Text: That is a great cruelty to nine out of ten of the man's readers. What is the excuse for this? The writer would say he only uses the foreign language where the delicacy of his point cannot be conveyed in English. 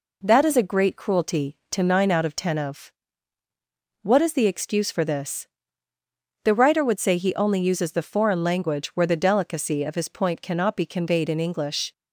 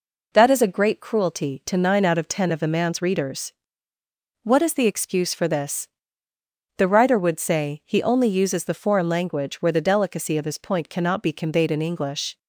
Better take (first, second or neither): second